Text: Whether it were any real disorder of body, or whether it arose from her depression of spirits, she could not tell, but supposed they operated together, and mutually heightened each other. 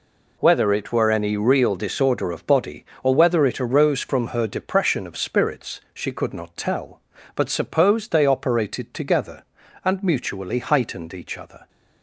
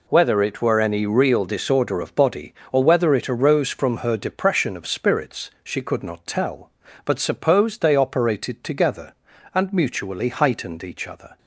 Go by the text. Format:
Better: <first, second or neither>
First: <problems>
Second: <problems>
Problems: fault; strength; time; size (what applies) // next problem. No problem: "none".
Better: neither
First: none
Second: none